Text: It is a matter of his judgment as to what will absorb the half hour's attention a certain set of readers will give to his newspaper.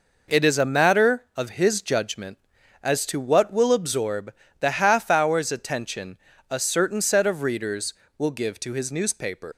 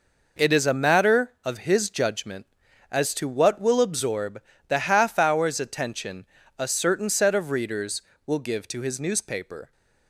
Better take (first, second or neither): second